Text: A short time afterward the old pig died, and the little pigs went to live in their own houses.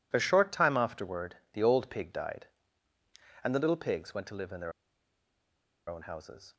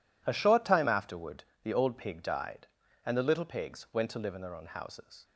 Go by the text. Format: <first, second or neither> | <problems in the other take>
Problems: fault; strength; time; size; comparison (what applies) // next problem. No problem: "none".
second | pauses between "afterward" and "the"; slight; at 1.3 s; 0.16 s long; slight in the second // pauses between "their" and "own"; at 4.7 s; 1.1 s long